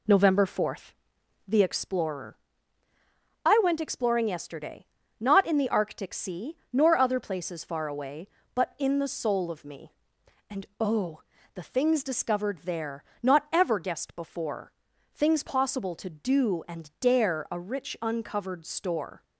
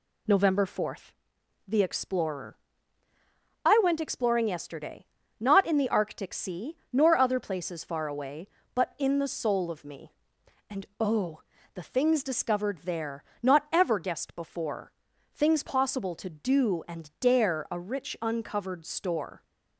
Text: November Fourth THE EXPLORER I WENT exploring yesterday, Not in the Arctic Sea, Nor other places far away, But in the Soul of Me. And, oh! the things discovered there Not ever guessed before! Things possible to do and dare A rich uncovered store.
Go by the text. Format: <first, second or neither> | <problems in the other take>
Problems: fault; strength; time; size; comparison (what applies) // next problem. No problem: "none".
second | starts louder than the rest; slight; until 1.9 s; 2.5 dB // pauses between "Fourth" and "THE"; noticeable; at 0.9 s; 0.56 s long; noticeable in the second // pauses between "EXPLORER" and "I"; at 2.3 s; 1.0 s long; also in the second // pauses between "there" and "Not"; slight; at 13.0 s; 0.22 s long; slight in the second